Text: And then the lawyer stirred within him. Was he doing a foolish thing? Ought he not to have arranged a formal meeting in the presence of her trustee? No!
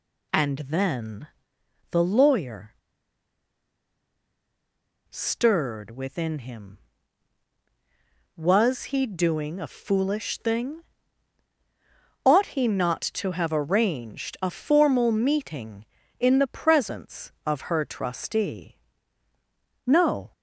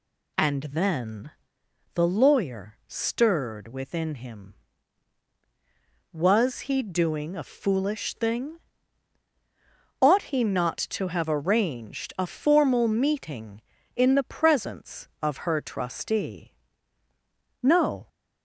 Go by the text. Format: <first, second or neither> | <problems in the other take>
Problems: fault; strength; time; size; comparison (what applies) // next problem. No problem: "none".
second | pauses between "then" and "the"; noticeable; at 1.2 s; 0.64 s long; noticeable in the second // pauses between "lawyer" and "stirred"; strong; at 2.7 s; 2.3 s long